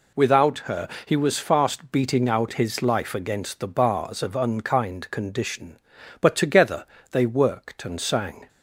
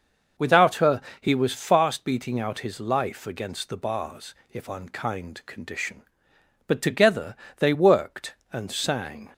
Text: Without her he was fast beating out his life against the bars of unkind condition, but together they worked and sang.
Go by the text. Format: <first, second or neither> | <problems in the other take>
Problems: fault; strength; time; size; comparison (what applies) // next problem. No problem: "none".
first | pauses between "her" and "he"; slight; at 1.0 s; 0.20 s long; slight in the first // says "if" for "of"; at 4.5 s // pauses between "together" and "they"; slight; at 7.3 s; 0.22 s long; slight in the first